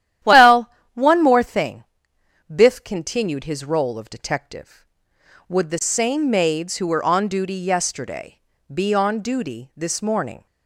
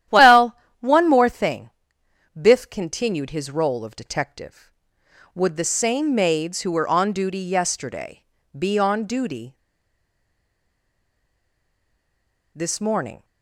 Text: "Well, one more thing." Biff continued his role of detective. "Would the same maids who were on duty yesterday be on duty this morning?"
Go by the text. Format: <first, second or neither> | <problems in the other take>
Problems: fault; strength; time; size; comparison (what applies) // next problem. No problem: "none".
first | starts louder than the rest; strong; until 1.3 s; 11.5 dB; strong in the first // pauses between "yesterday" and "be"; slight; at 8.2 s; 0.34 s long; slight in the first // pauses between "duty" and "this"; strong; at 9.5 s; 3.0 s long